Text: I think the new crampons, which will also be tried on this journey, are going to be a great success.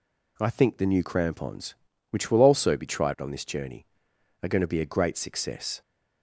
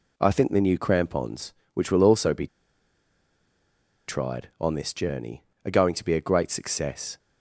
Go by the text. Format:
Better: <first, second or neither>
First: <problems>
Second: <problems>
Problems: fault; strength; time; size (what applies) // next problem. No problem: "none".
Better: first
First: none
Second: pauses between "be" and "tried"; strong; at 2.4 s; 1.6 s long